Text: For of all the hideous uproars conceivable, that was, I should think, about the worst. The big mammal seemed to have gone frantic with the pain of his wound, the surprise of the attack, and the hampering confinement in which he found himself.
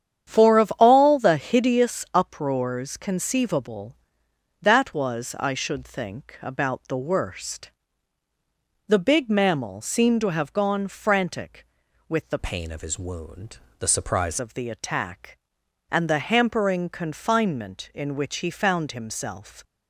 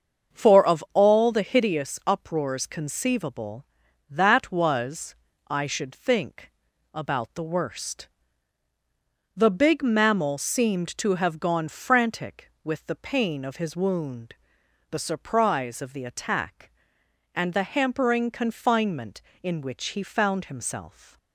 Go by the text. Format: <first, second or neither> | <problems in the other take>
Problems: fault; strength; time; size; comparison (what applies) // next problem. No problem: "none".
second | starts louder than the rest; strong; until 1.3 s; 9 dB; also in the second // changes voice from "pain" to "surprise"; from 12.3 to 14.3 s; 2.0 s long